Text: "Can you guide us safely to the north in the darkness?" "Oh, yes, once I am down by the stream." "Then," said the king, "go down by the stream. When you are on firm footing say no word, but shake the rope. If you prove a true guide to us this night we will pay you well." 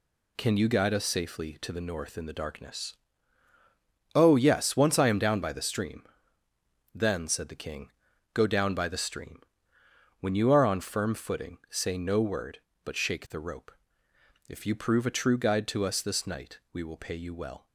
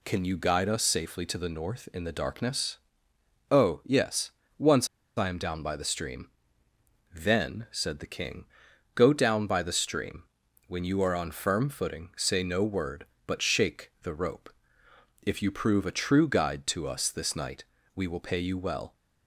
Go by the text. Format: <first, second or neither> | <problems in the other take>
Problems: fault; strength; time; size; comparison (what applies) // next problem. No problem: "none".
first | pauses between "once" and "I"; slight; at 4.8 s; 0.29 s long // pauses between "night" and "we"; slight; at 17.6 s; 0.32 s long